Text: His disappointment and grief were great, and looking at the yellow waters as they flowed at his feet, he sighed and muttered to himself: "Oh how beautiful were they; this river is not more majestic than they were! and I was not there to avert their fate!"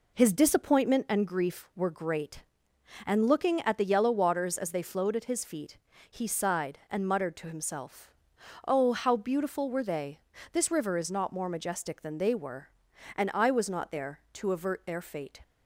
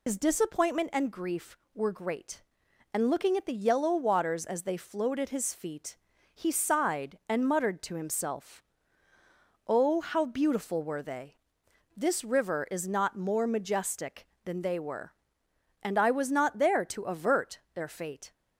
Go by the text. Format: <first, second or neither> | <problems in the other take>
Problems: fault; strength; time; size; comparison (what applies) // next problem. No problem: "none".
first | loses the start of "His"; at 0.0 s; 110 ms